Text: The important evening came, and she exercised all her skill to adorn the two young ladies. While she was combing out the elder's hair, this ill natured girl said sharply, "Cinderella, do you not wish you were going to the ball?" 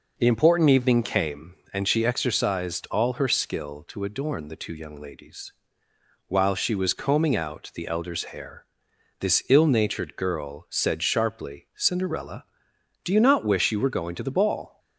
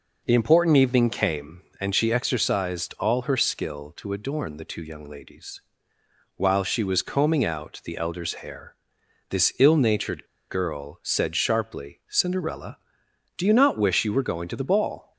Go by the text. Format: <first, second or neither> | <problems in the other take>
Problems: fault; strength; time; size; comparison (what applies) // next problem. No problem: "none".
first | pauses between "natured" and "girl"; slight; at 10.2 s; 0.24 s long